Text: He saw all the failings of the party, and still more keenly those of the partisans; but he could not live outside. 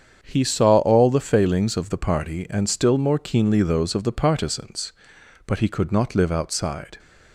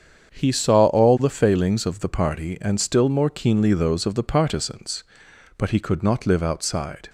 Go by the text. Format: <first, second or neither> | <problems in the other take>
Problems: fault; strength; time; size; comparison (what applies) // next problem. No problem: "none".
neither | starts louder than the rest; strong; the same in both